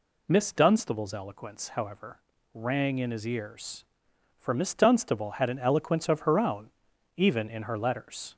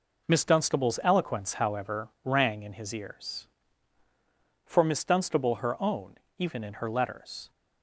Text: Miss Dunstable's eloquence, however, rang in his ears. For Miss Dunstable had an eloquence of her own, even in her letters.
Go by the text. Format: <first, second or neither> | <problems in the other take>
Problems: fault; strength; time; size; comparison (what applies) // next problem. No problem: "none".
first | skips "had an eloquence of"; at 5.5 s